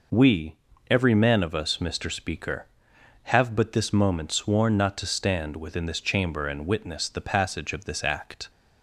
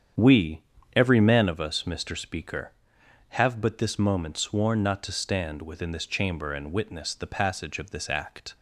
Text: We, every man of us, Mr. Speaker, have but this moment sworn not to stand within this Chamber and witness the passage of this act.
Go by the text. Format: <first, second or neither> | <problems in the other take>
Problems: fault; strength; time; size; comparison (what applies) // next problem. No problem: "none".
first | starts louder than the rest; strong; until 1.7 s; 8 dB